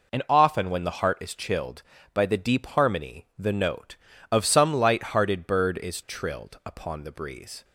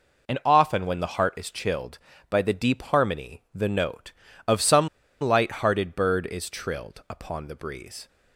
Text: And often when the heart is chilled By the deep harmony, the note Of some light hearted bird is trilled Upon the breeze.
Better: first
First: none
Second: pauses between "some" and "light"; slight; at 4.8 s; 0.33 s long

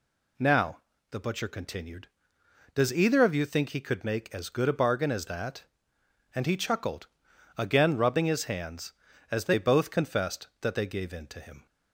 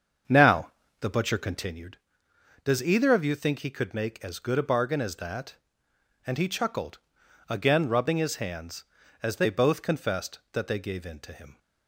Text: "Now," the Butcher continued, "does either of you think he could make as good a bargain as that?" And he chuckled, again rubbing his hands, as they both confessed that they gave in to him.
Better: first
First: none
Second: starts louder than the rest; until 1.8 s; 7 dB

